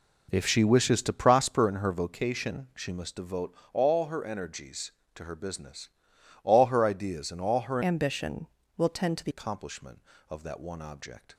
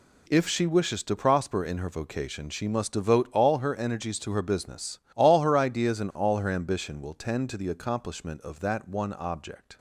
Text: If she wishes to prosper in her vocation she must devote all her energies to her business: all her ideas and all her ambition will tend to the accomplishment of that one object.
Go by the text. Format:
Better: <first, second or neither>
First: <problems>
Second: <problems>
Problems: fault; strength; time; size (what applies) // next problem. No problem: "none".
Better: second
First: pauses between "devote" and "all"; slight; at 3.5 s; 0.22 s long // changes voice from "ambition" to "the"; from 7.8 to 9.3 s; 1.5 s long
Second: none